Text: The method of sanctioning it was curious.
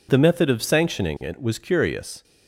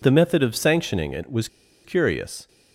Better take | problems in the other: first | pauses between "was" and "curious"; at 1.4 s; 0.37 s long

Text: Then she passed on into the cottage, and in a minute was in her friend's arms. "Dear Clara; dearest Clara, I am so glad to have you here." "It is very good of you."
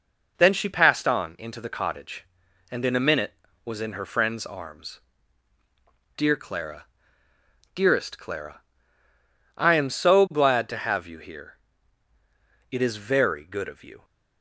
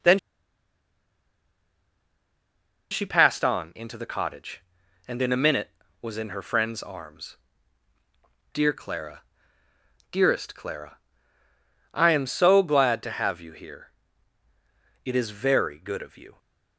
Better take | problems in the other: first | pauses between "Then" and "she"; strong; at 0.1 s; 2.7 s long

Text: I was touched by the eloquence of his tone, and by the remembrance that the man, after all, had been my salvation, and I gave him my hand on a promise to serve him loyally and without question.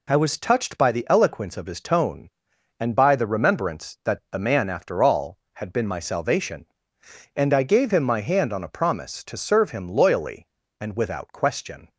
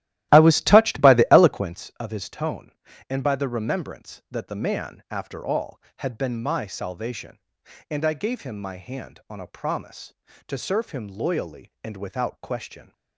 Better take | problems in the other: first | starts louder than the rest; strong; until 1.7 s; 15 dB

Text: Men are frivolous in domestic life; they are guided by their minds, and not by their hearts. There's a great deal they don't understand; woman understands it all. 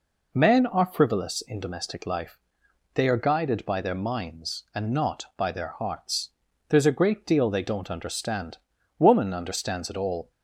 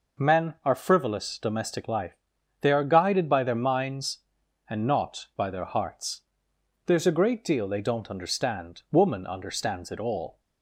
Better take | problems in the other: first | skips "in"; at 1.3 s

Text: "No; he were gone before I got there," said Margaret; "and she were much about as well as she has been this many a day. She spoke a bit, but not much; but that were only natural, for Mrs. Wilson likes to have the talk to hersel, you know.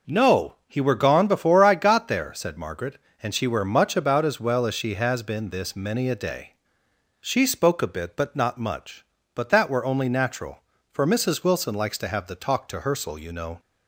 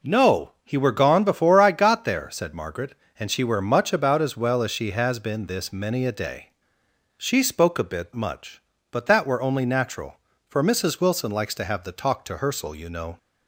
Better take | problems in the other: first | skips "but not"; at 8.1 s

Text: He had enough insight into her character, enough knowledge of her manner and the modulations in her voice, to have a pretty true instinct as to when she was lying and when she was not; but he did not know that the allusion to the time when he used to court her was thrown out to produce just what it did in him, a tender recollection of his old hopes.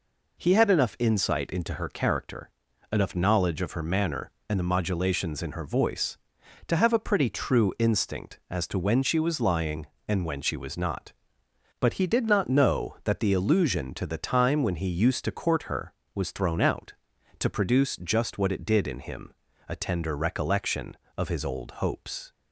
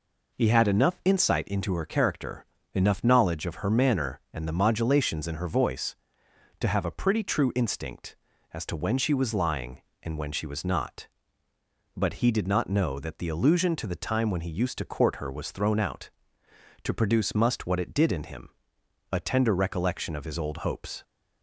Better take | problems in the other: first | says "must" for "just"; at 17.3 s

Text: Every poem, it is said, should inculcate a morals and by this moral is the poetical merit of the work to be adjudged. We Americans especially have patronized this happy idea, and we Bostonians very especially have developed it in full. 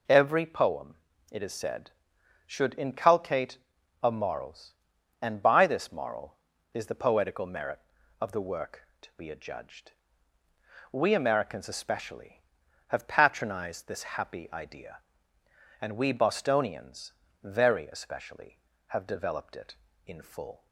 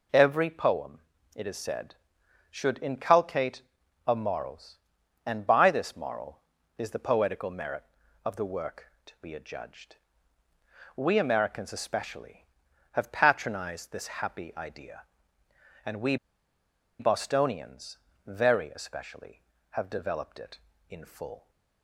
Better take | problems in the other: first | pauses between "inculcate" and "a"; noticeable; at 3.6 s; 0.46 s long; noticeable in the first // pauses between "we" and "Bostonians"; noticeable; at 16.1 s; 0.84 s long // pauses between "Bostonians" and "very"; slight; at 17.9 s; 0.28 s long; slight in the first

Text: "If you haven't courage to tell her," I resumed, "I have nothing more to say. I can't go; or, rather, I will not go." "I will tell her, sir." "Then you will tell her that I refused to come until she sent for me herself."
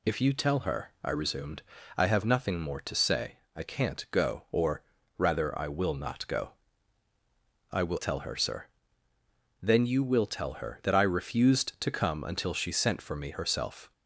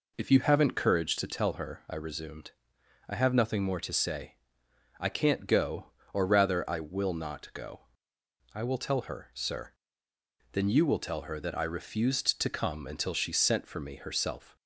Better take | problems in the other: second | skips "haven't courage to"; at 0.3 s

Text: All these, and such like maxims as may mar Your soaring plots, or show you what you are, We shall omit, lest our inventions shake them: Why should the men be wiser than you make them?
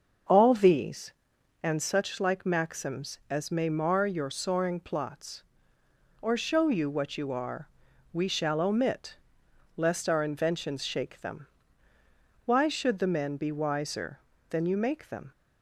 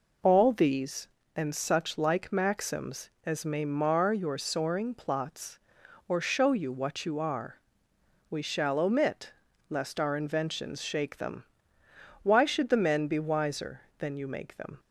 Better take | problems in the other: second | starts louder than the rest; until 1.6 s; 6.5 dB

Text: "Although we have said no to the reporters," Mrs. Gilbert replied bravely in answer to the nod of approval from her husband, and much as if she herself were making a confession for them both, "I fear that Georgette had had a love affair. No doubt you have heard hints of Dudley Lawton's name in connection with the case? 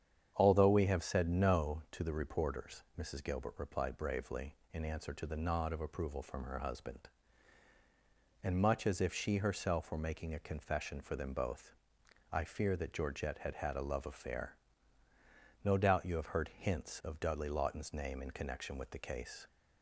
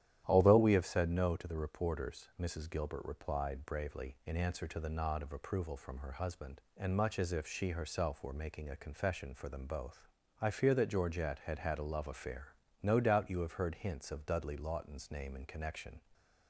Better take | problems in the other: first | starts louder than the rest; strong; until 1.2 s; 11.5 dB; strong in the first // stops before "with the case"; at 16.1 s

